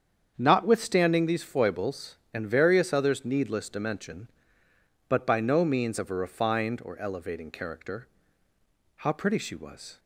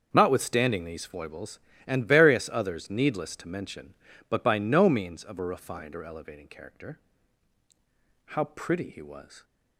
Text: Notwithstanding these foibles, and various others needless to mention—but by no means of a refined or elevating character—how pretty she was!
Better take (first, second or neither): first